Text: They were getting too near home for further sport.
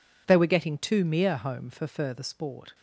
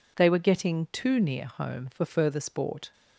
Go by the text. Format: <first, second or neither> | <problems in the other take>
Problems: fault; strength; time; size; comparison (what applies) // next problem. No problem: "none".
second | says "mere" for "near"; at 1.0 s